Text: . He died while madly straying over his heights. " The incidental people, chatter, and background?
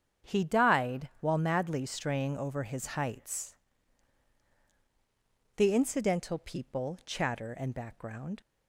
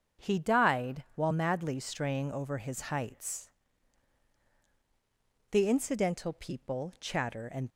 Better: first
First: starts louder than the rest; strong; until 1.3 s; 9 dB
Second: starts louder than the rest; strong; until 1.3 s; 8.5 dB // stops before "background"; at 7.6 s

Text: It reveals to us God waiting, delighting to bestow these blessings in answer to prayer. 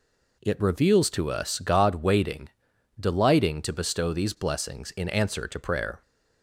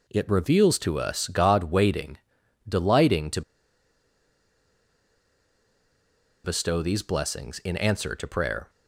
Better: first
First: none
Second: pauses between "to" and "bestow"; strong; at 3.4 s; 3.0 s long

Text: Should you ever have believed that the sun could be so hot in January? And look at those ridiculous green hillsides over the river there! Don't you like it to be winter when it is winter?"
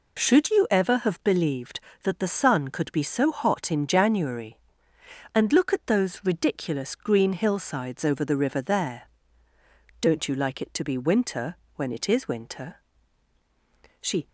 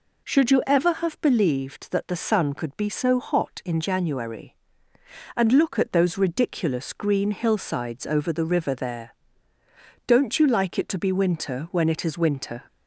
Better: second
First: pauses between "winter" and "when"; slight; at 11.5 s; 0.20 s long // goes on to say "She"; slight; from 14.0 s on; 0.26 s long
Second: none

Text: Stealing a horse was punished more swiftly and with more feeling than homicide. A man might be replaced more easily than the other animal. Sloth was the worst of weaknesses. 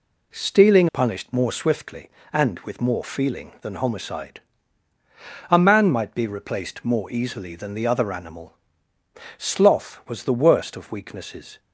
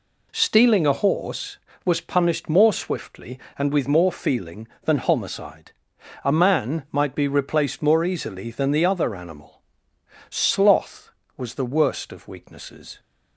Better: second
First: skips "a horse was"; at 0.8 s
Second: none

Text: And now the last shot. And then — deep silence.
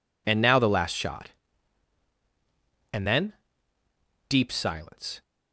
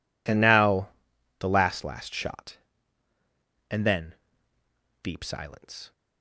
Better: first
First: none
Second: pauses between "now" and "the"; noticeable; at 0.8 s; 0.50 s long // says "last" twice; at 1.8 s

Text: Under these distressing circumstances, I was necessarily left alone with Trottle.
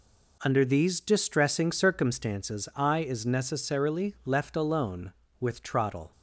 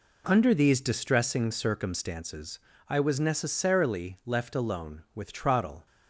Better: second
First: says "is" for "was"; at 2.9 s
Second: none

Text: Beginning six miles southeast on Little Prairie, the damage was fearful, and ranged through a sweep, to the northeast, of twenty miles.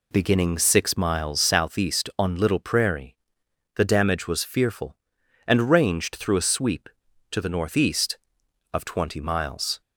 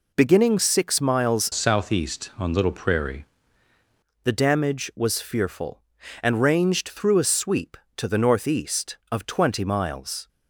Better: first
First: none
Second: changes voice from "southeast" to "Prairie"; from 1.5 to 3.2 s; 1.7 s long

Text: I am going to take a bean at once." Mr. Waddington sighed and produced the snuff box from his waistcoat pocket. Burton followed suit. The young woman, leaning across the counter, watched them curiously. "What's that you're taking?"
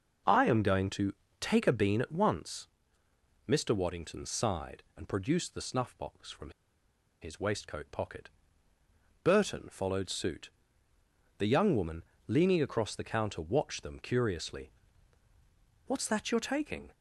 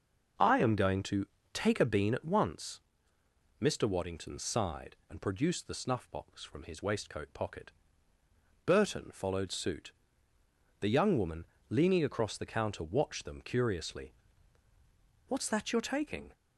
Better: second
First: starts louder than the rest; until 1.5 s; 6.5 dB // pauses between "to" and "take"; slight; at 1.1 s; 0.28 s long // pauses between "from" and "his"; noticeable; at 6.5 s; 0.70 s long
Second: starts louder than the rest; until 1.7 s; 6.5 dB // pauses between "to" and "take"; slight; at 1.2 s; 0.28 s long

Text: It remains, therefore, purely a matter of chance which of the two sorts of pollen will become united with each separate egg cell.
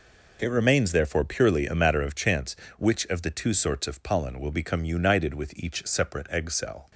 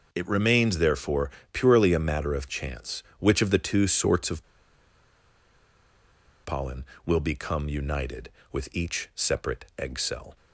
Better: first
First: none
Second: pauses between "of" and "pollen"; strong; at 4.4 s; 2.0 s long

